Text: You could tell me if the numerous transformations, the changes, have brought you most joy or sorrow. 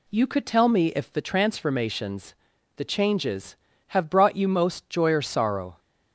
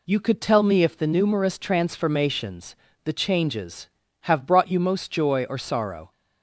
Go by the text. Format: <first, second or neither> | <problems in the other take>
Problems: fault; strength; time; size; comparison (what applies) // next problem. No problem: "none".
second | skips "numerous"; at 1.2 s